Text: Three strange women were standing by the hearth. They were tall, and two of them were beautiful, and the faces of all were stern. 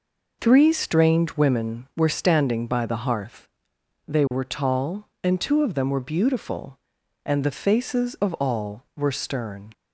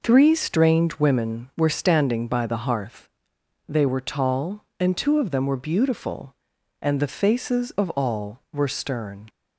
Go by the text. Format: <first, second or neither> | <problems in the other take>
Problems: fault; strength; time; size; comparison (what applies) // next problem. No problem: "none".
neither | none